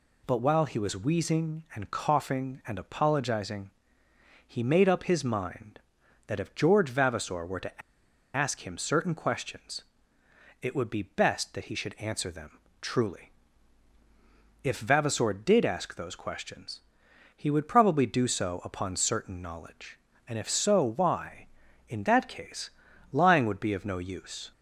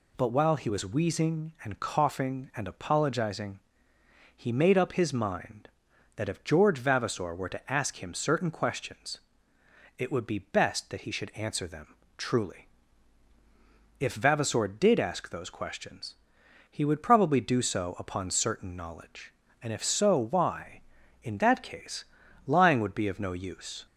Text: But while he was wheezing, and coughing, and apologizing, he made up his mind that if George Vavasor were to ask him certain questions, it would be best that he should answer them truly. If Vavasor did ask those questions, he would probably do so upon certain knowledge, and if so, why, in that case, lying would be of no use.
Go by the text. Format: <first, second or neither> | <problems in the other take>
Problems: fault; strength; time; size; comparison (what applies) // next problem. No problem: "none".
second | pauses between "to" and "ask"; noticeable; at 7.8 s; 0.54 s long // pauses between "them" and "truly"; slight; at 12.5 s; 0.24 s long; slight in the second